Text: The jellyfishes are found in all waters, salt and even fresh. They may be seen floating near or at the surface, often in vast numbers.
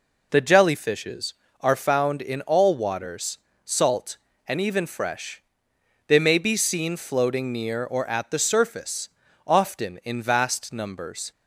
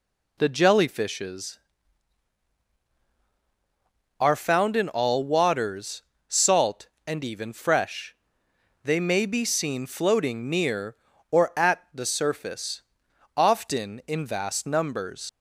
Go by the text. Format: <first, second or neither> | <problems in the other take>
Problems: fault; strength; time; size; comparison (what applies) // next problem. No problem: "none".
first | leaves "numbers" unfinished; at 15.2 s; 95 ms